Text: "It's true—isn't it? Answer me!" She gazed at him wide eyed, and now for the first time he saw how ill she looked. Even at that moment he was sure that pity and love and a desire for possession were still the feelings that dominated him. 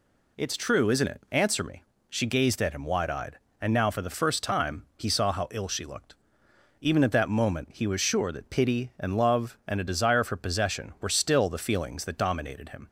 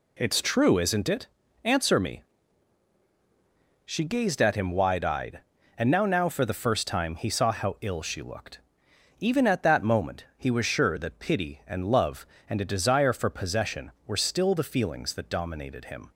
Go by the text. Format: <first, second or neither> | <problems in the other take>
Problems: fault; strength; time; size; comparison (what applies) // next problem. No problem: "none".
first | says "now" twice; at 6.0 s